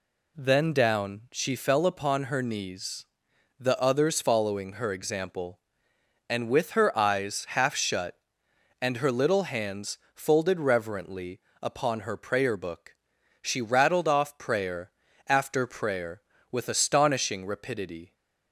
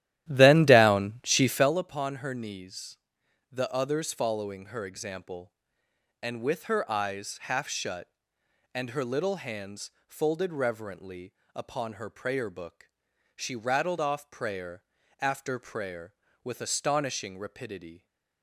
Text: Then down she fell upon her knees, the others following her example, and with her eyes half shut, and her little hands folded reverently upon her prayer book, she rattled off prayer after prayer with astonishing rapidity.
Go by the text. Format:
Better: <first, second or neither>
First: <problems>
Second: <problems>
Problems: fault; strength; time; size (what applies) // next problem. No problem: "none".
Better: first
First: pauses between "hands" and "folded"; slight; at 9.9 s; 0.16 s long // pauses between "reverently" and "upon"; slight; at 11.4 s; 0.22 s long // pauses between "prayer" and "after"; at 14.8 s; 0.38 s long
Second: starts louder than the rest; strong; until 1.8 s; 13 dB // pauses between "hands" and "folded"; slight; at 9.8 s; 0.16 s long // pauses between "reverently" and "upon"; slight; at 11.3 s; 0.22 s long // pauses between "prayer" and "after"; at 14.8 s; 0.38 s long